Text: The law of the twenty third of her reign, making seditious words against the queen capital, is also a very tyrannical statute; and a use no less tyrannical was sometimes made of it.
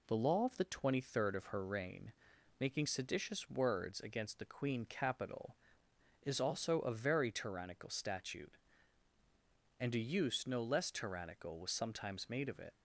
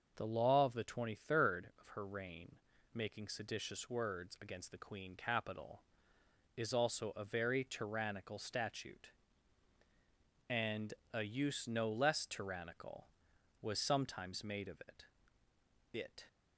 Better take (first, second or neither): first